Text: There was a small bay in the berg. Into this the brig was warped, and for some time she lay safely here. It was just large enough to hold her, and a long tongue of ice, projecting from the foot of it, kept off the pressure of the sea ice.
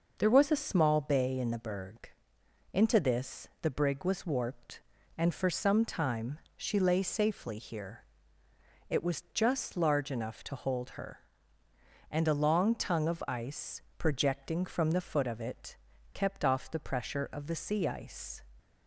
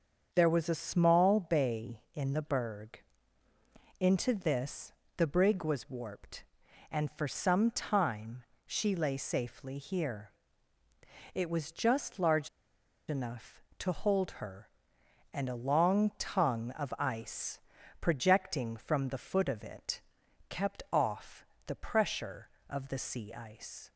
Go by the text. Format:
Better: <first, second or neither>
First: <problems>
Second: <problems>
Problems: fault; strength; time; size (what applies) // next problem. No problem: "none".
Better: first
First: pauses between "time" and "she"; slight; at 6.3 s; 0.18 s long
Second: starts louder than the rest; until 1.3 s; 7 dB // pauses between "this" and "the"; slight; at 4.9 s; 0.24 s long // pauses between "time" and "she"; slight; at 8.4 s; 0.22 s long // pauses between "large" and "enough"; noticeable; at 12.4 s; 0.59 s long // pauses between "off" and "the"; slight; at 21.4 s; 0.22 s long